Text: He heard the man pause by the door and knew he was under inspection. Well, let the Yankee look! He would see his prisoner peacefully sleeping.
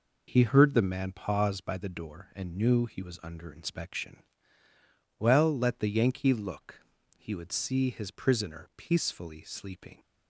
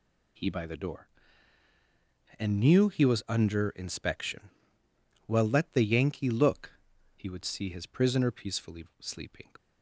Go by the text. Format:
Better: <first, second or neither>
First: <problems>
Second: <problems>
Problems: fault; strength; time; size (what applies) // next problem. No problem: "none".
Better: first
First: none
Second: skips "heard the man pause"; at 0.5 s // pauses between "peacefully" and "sleeping"; slight; at 8.8 s; 0.15 s long